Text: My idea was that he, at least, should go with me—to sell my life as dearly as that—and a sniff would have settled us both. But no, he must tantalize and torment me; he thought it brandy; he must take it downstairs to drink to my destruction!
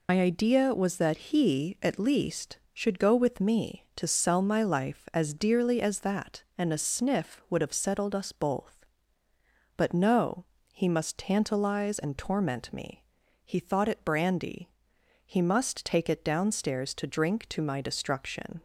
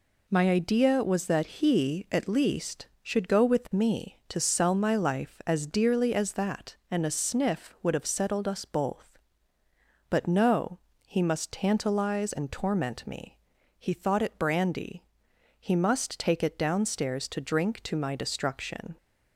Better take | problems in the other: second | loses the start of "My"; at 0.0 s; 95 ms

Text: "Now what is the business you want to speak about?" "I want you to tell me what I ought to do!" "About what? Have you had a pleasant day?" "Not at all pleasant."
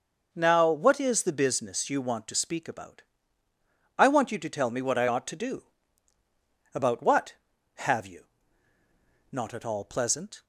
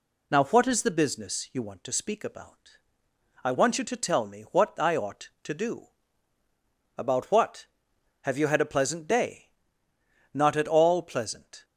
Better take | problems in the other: second | skips "had a pleasant day"; at 8.7 s

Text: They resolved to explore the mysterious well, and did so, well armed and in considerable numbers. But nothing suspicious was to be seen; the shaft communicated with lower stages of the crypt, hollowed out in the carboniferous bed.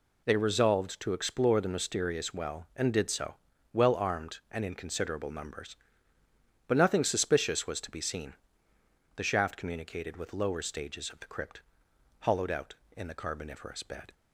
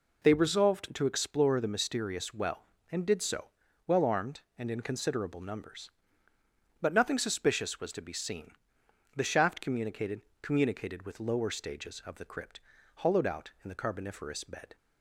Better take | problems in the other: first | says "communicated" twice; at 10.4 s

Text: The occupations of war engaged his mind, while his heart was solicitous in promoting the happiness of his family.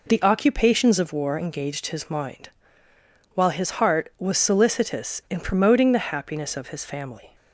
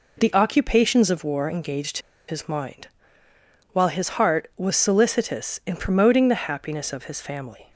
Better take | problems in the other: first | pauses between "engaged" and "his"; slight; at 1.9 s; 0.30 s long

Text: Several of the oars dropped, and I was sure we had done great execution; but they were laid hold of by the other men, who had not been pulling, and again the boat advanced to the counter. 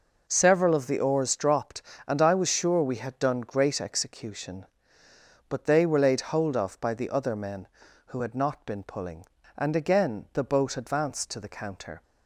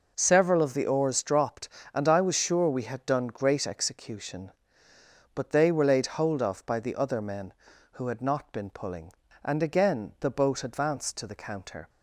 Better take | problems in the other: neither | none

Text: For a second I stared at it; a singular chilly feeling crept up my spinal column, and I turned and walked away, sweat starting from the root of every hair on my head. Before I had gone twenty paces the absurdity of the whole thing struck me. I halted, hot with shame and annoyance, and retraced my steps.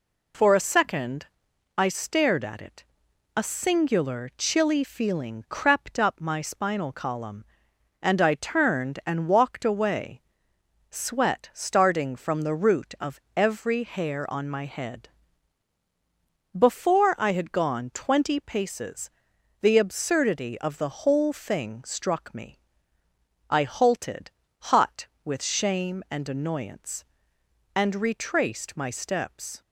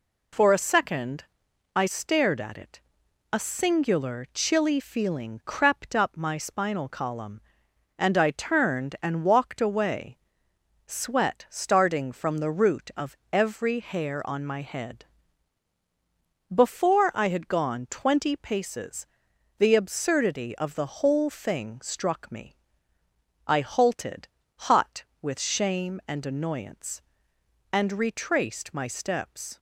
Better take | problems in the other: neither | pauses between "second" and "I"; noticeable; the same in both // pauses between "of" and "every"; slight; the same in both // pauses between "paces" and "the"; noticeable; the same in both

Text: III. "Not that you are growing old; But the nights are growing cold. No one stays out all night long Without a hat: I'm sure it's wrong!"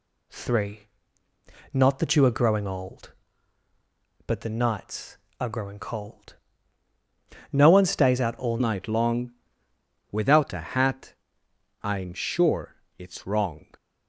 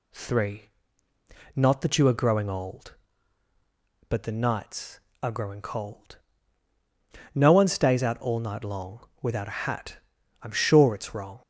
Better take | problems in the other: second | changes voice at "night"; from 8.5 s on; 5.1 s long // pauses between "long" and "Without"; noticeable; at 9.3 s; 0.80 s long // pauses between "sure" and "it's"; slight; at 12.7 s; 0.22 s long

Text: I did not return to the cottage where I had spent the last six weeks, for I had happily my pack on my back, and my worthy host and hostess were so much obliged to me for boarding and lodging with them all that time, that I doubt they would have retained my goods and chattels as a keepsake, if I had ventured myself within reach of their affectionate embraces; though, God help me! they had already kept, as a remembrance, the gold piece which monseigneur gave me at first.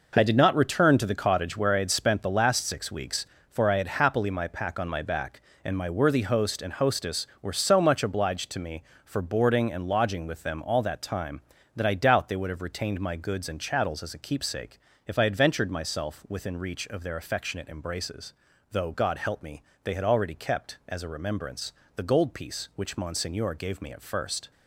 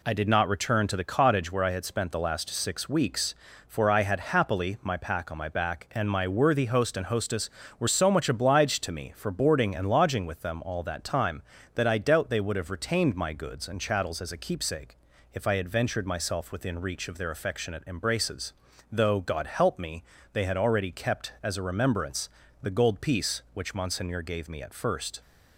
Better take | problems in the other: neither | none

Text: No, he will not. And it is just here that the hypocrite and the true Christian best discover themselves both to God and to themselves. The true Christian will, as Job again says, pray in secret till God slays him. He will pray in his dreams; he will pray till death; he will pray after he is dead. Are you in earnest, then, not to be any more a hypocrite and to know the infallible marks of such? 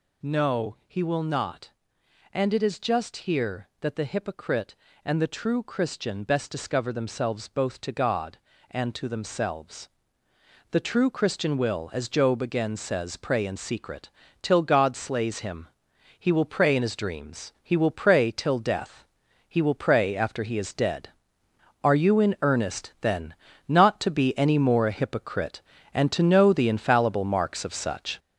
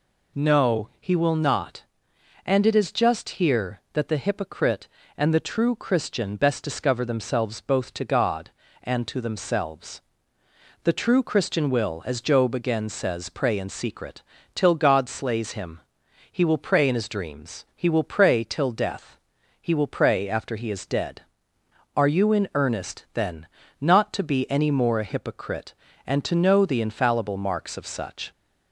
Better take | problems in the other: second | gets louder; noticeable; throughout; 6 dB // pauses between "secret" and "till"; slight; at 14.0 s; 0.32 s long; slight in the second

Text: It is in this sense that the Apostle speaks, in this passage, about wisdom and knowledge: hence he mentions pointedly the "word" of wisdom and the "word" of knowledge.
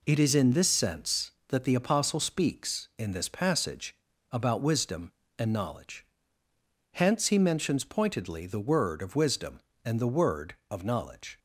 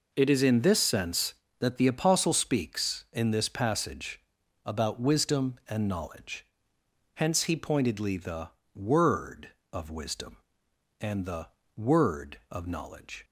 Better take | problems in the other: first | skips "mentions"; at 7.5 s // pauses between "the" and "word"; slight; at 8.5 s; 0.24 s long // pauses between "the" and "word"; slight; at 11.4 s; 0.30 s long

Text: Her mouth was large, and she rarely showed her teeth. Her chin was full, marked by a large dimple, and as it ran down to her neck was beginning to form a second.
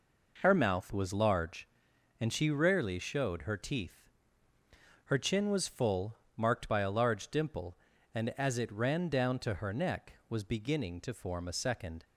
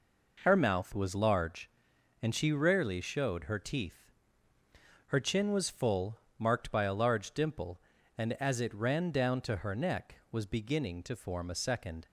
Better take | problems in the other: neither | none

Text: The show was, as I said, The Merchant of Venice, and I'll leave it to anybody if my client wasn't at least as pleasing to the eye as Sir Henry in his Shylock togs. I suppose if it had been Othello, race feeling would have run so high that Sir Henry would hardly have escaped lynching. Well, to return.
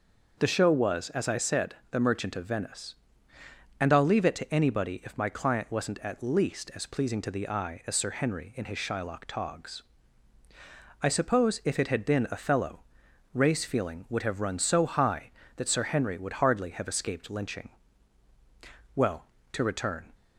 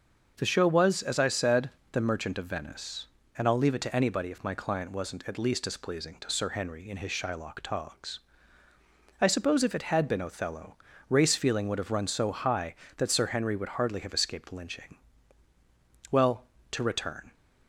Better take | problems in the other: first | starts louder than the rest; noticeable; until 1.3 s; 6 dB // skips "the eye as"; at 6.2 s

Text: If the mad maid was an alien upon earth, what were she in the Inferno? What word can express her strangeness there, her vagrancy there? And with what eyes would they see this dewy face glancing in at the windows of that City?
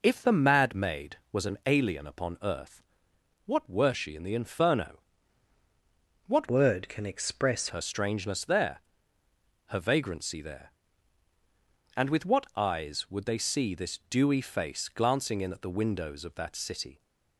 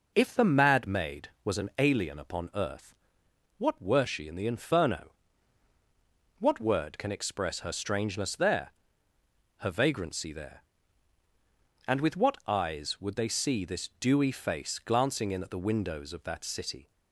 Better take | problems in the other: second | changes voice from "word" to "express"; from 6.4 to 7.6 s; 1.2 s long

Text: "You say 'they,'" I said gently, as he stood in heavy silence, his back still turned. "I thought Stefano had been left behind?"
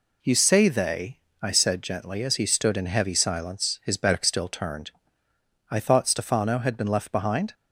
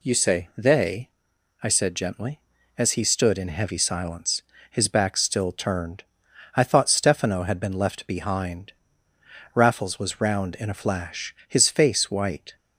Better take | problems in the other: first | goes on to say "Raffles was round in a flash his face white"; strong; from 9.5 s on; 3.0 s long

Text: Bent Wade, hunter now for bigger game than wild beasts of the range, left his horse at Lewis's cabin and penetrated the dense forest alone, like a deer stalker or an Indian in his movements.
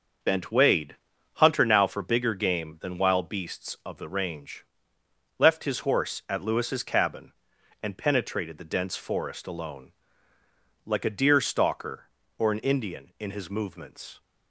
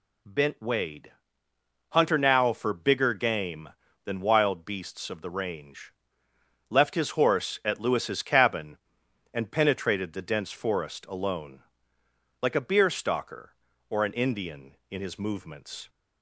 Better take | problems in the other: first | says "beer" for "deer"; at 12.6 s

